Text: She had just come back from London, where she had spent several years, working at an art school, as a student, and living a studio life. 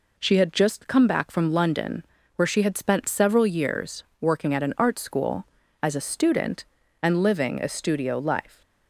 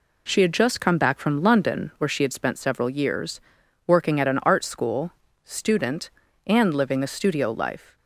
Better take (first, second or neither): first